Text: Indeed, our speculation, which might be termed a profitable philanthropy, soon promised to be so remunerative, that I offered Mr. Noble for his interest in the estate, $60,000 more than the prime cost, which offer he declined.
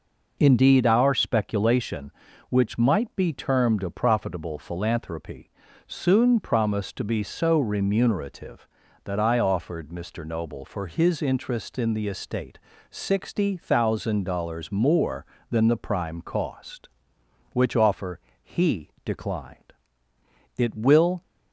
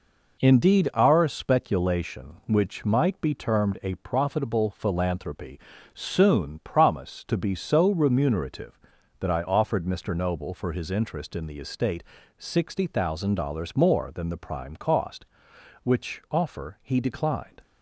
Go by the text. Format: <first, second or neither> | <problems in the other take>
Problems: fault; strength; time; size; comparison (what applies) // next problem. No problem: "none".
second | pauses between "offer" and "he"; slight; at 18.2 s; 0.32 s long // pauses between "he" and "declined"; slight; at 18.9 s; 0.16 s long // goes on to say "It will"; noticeable; from 20.5 s on; 0.64 s long